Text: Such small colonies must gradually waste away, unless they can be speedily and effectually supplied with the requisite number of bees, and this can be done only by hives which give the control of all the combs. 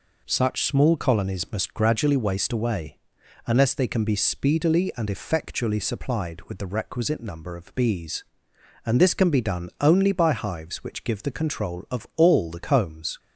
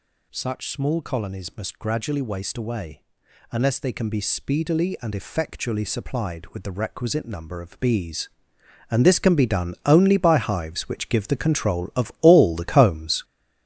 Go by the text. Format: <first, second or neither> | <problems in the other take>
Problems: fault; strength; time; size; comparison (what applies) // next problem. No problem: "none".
first | gets louder; strong; throughout; 7.5 dB